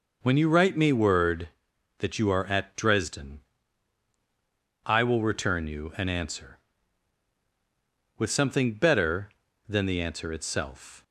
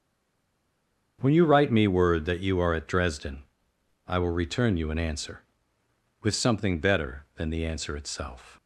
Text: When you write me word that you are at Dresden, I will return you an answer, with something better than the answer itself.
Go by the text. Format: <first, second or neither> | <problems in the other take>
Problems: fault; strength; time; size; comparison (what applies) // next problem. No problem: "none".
first | stays silent before the first word; noticeable; until 1.1 s; 1.1 s long // starts louder than the rest; strong; until 2.2 s; 7 dB